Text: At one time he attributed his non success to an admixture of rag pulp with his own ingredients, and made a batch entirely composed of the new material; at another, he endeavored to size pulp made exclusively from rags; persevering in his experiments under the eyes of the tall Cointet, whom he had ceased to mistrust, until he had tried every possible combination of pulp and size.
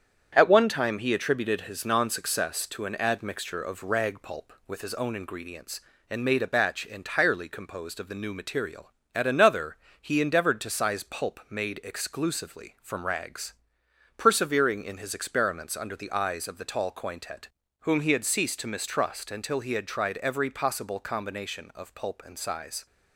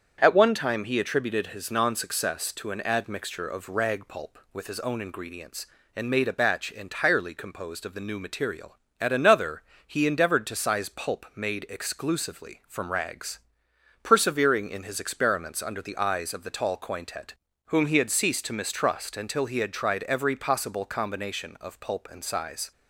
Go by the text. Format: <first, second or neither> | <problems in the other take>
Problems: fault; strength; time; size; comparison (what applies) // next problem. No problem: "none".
second | gets quieter; noticeable; throughout; 4 dB // starts louder than the rest; strong; until 1.3 s; 8 dB; strong in the second